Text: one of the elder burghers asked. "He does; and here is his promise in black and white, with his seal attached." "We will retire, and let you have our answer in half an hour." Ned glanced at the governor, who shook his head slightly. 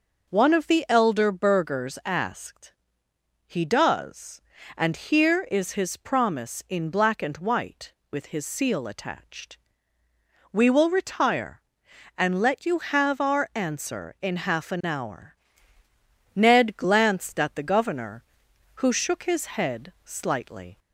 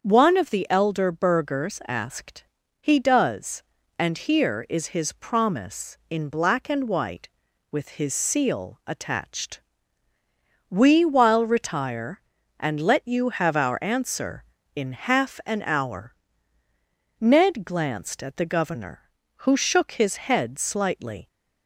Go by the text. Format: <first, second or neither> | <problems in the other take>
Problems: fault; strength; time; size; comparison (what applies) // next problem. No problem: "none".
first | starts louder than the rest; until 1.0 s; 7 dB // says "while" for "will"; at 11.0 s